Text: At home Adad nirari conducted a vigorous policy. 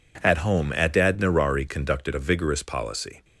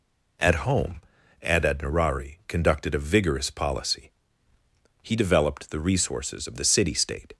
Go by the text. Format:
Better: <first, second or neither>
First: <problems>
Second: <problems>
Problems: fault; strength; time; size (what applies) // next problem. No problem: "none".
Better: first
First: none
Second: pauses between "home" and "Adad"; at 0.9 s; 0.42 s long // goes on to say "He developed the resources of the city state"; strong; from 5.0 s on; 2.3 s long